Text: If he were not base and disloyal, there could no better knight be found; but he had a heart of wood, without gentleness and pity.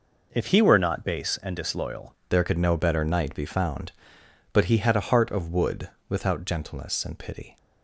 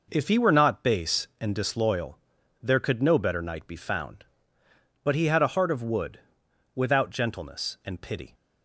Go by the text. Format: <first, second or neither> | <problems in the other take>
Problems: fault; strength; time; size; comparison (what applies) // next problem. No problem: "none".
second | changes voice at "there"; from 2.3 s on; 5.2 s long